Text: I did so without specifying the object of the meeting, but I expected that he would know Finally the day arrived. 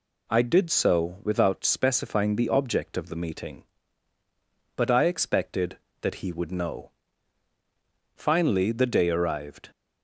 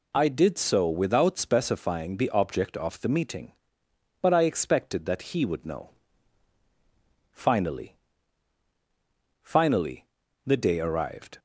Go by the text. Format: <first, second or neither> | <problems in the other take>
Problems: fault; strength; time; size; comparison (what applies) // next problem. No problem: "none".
first | pauses between "know" and "Finally"; strong; at 5.9 s; 1.4 s long; also in the first // says "Finally" twice; at 9.4 s